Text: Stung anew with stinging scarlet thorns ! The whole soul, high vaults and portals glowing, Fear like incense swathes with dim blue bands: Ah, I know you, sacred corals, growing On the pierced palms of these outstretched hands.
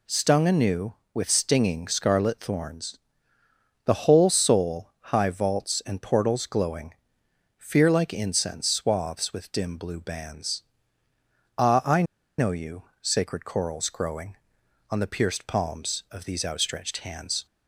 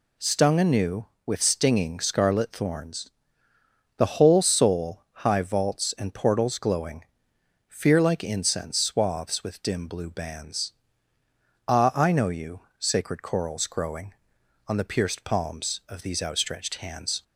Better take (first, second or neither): second